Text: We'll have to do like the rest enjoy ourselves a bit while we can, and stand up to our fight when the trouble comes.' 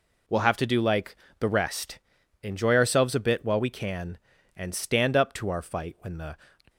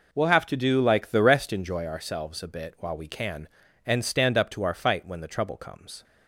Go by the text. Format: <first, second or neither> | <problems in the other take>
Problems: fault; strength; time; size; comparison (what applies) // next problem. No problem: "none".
second | pauses between "like" and "the"; slight; at 1.1 s; 0.22 s long // pauses between "rest" and "enjoy"; at 1.9 s; 0.44 s long // stops before "trouble comes"; at 6.6 s